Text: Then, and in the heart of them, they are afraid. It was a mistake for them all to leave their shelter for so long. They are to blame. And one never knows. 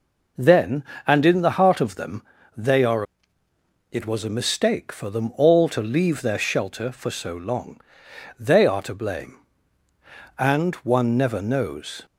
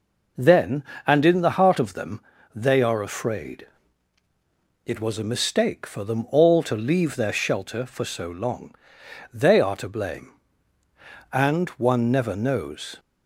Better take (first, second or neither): second